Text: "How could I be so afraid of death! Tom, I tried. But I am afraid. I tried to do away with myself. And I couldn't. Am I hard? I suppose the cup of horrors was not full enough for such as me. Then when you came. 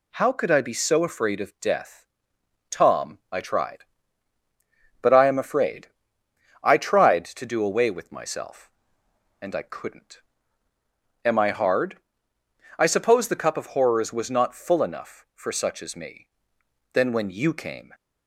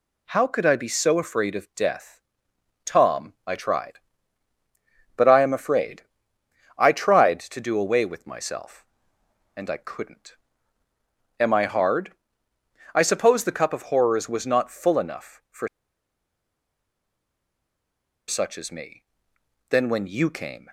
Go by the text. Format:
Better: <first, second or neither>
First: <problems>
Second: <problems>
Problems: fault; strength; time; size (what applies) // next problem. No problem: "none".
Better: first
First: none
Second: pauses between "for" and "such"; strong; at 15.6 s; 2.5 s long